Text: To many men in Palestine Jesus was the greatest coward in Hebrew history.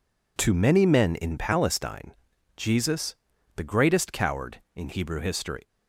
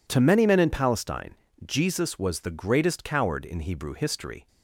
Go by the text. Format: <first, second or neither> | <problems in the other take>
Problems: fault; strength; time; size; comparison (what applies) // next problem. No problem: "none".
second | pauses between "Palestine" and "Jesus"; at 2.1 s; 0.44 s long; slight in the second // skips "was"; at 3.3 s